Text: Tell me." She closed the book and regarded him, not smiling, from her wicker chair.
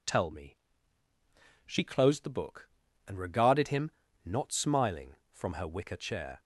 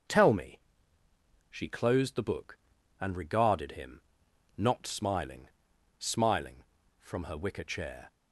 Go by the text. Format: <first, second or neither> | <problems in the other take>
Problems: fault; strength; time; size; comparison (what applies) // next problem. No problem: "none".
first | starts louder than the rest; until 2.0 s; 6.5 dB // says "smiling" twice; at 6.0 s